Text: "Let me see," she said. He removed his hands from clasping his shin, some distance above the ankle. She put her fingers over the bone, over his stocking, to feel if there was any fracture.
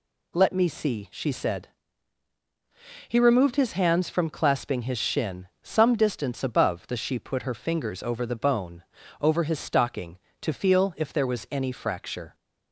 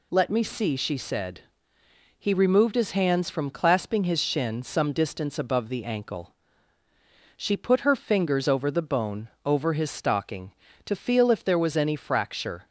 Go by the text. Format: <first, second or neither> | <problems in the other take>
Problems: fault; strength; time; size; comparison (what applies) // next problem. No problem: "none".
second | skips "ankle"; at 6.9 s